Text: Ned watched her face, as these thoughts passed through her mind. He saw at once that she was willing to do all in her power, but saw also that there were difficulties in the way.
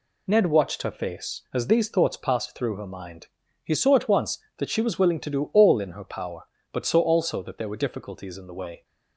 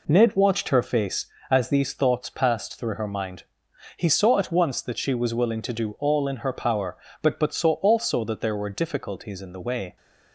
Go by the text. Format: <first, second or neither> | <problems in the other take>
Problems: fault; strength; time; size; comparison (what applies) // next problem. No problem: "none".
first | says "but" twice; at 7.3 s